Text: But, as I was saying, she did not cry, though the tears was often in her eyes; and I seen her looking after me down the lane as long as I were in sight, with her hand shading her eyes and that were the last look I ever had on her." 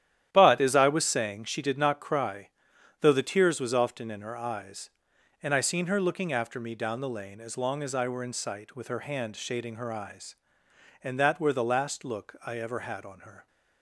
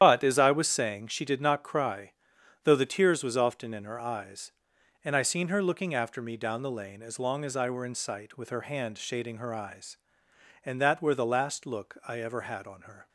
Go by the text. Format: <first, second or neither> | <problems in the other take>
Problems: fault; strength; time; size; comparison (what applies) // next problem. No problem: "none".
first | loses the start of "But"; at 0.0 s; 75 ms // starts louder than the rest; strong; until 1.0 s; 10.5 dB; strong in the first